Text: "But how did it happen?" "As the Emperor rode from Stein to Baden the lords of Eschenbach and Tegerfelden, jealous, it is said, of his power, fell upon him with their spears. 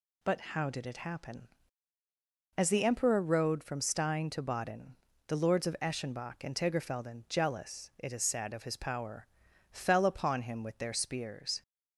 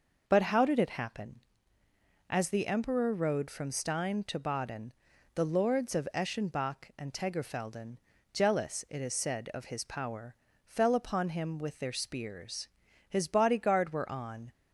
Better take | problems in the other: first | pauses between "Baden" and "the"; at 4.9 s; 0.44 s long; slight in the first // goes on to say "His bodyguard were on"; from 13.0 s on; 1.4 s long

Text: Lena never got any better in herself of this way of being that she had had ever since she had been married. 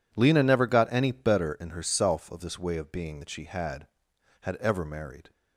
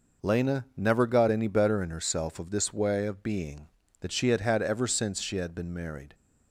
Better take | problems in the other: second | skips "since she had been"; at 4.8 s

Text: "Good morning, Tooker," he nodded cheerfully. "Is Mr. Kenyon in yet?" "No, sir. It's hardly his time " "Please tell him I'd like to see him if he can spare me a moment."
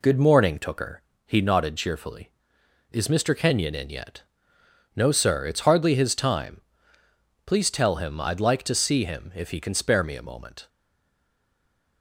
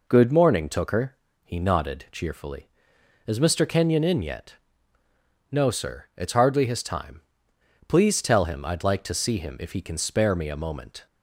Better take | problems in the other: second | stays silent after the last word; noticeable; from 10.6 s on; 1.4 s long

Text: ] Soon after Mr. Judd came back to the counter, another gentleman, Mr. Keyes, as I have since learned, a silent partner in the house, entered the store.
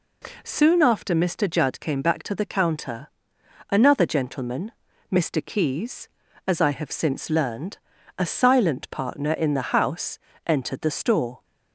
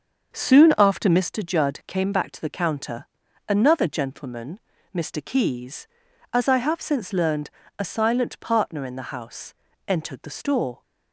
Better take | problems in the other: first | starts louder than the rest; until 1.4 s; 6.5 dB

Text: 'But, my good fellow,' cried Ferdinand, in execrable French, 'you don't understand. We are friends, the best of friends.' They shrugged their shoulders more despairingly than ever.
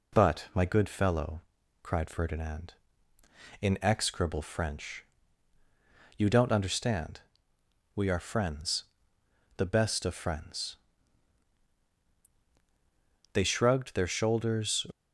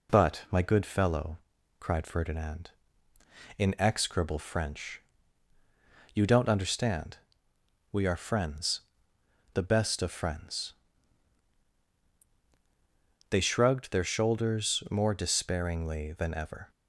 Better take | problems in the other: second | stops before "more despairingly than ever"; at 14.9 s

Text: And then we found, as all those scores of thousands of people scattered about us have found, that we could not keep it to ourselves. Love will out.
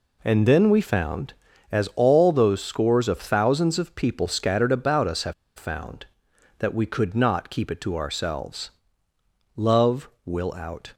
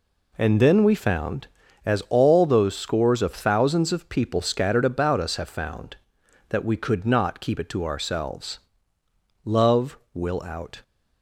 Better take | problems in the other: second | pauses between "have" and "found"; slight; at 5.3 s; 0.24 s long

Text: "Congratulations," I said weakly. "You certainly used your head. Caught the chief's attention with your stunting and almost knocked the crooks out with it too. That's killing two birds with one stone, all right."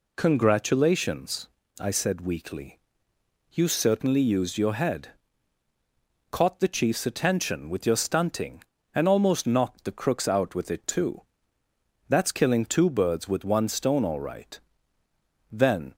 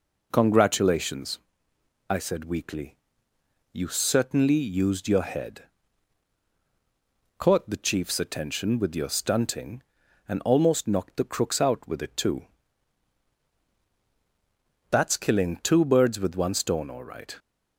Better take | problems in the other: second | goes on to say "Then"; slight; from 15.5 s on; 0.44 s long

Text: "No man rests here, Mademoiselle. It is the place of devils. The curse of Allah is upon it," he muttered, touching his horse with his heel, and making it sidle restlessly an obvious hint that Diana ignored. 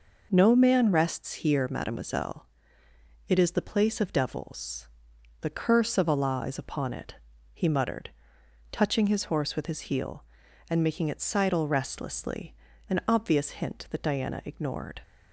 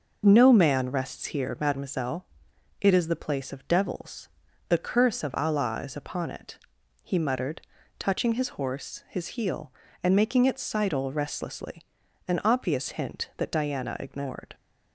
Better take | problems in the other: first | skips "with"; at 9.0 s // pauses between "restlessly" and "an"; at 11.8 s; 0.44 s long; slight in the first

